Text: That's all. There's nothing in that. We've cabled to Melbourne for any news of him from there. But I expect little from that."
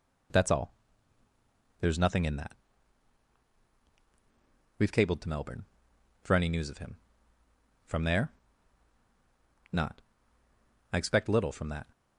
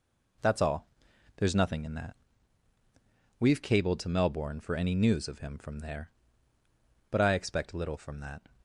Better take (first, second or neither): second